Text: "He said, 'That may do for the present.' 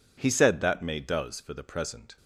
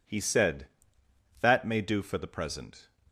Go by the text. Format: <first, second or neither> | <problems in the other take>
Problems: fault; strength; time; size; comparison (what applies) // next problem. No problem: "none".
second | says "does" for "do"; at 0.9 s